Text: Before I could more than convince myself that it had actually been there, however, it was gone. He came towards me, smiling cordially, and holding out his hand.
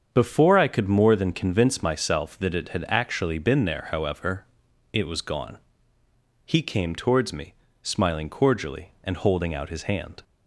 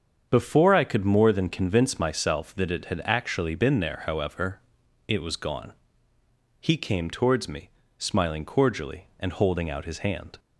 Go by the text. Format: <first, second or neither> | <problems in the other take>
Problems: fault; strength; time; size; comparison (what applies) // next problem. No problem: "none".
neither | starts louder than the rest; strong; the same in both